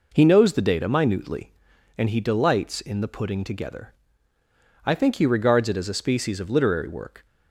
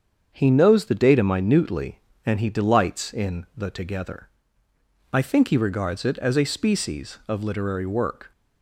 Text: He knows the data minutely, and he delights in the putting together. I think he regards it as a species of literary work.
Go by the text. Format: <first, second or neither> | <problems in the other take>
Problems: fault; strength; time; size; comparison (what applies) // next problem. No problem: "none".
first | starts louder than the rest; strong; until 1.3 s; 7 dB // skips "putting"; at 3.6 s